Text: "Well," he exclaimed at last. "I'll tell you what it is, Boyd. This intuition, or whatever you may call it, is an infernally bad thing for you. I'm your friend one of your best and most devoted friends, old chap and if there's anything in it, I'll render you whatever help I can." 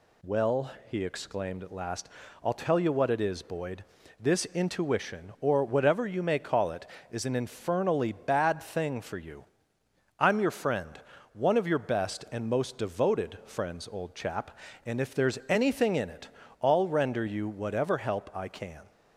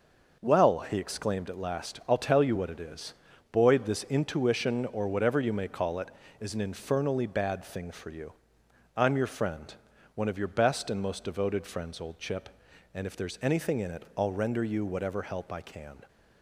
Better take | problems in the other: first | pauses between "friend" and "one"; at 9.7 s; 0.40 s long; slight in the first // says "chip" for "chap"; at 12.1 s

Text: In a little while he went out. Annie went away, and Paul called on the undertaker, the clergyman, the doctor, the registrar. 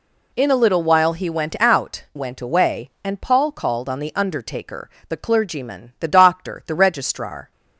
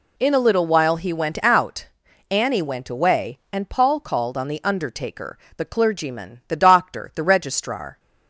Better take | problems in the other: second | skips "Annie"; at 2.0 s

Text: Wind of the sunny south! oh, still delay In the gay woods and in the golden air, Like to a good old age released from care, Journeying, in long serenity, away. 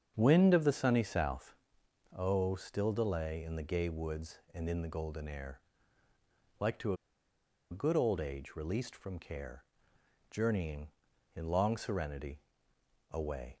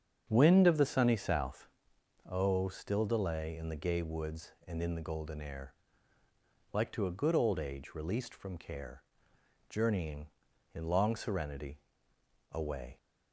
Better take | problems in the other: second | starts louder than the rest; strong; until 1.1 s; 7.5 dB; strong in the second // pauses between "a" and "good"; noticeable; at 6.9 s; 0.76 s long

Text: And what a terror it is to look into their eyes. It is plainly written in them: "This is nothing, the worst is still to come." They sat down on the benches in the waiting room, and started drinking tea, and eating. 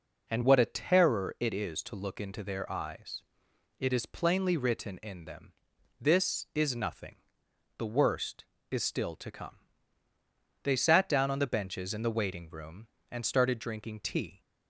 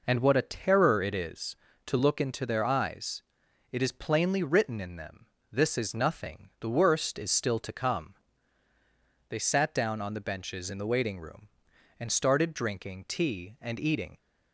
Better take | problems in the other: second | stops before "and eating"; at 14.4 s

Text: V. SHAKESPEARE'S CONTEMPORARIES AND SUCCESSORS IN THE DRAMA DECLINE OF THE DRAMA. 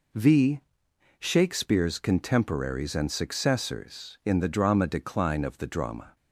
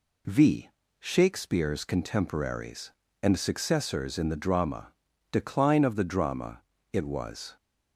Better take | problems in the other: first | pauses between "DRAMA" and "DECLINE"; at 4.9 s; 0.38 s long // goes on to say "It was"; noticeable; from 6.9 s on; 0.64 s long

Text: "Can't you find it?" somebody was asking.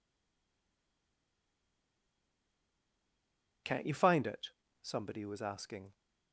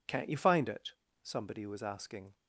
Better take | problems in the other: second | stays silent before the first word; strong; until 3.6 s; 3.6 s long

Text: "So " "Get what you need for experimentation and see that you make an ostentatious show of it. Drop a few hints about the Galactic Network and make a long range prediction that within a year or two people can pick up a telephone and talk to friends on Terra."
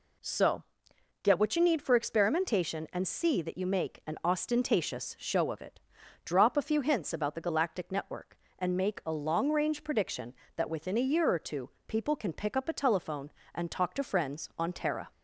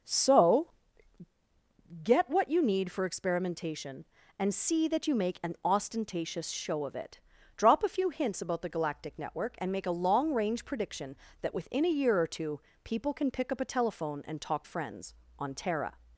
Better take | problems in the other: first | pauses between "two" and "people"; slight; at 12.5 s; 0.24 s long; slight in the first // skips "to"; at 14.6 s

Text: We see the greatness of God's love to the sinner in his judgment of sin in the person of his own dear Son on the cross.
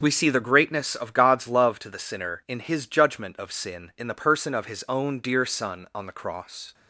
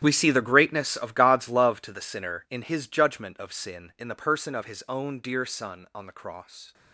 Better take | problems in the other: first | gets quieter; strong; throughout; 16 dB // starts louder than the rest; strong; until 1.0 s; 11 dB; also in the first

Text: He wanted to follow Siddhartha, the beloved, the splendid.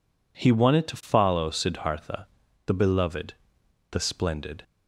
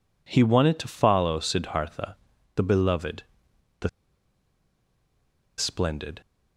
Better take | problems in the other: first | pauses between "the" and "splendid"; strong; at 3.8 s; 1.7 s long

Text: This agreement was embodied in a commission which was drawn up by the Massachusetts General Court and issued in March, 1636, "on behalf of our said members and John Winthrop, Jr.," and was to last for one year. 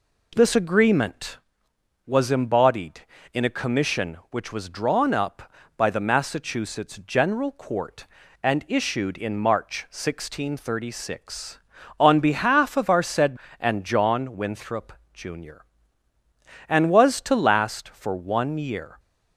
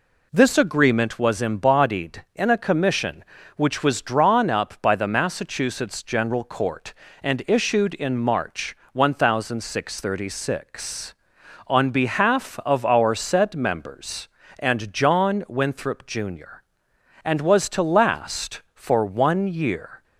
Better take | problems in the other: second | skips "members"; at 13.4 s

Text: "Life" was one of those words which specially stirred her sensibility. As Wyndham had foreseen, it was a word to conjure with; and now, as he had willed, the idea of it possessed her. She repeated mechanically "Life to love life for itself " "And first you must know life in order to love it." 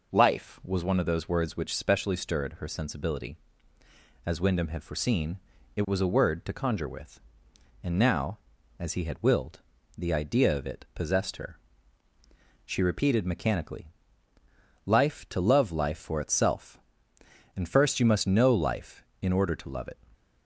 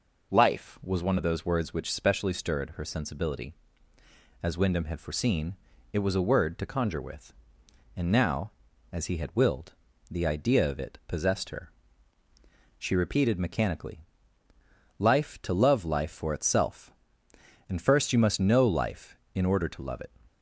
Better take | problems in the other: neither | pauses between "mechanically" and "Life"; noticeable; the same in both

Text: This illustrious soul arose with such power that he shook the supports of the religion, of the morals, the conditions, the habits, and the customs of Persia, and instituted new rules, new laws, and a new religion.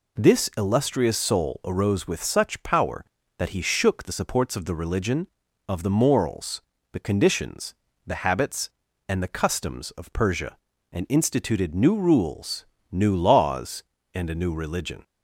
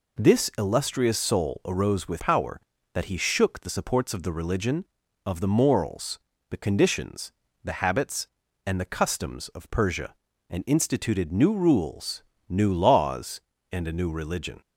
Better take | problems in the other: first | skips "such"; at 2.1 s

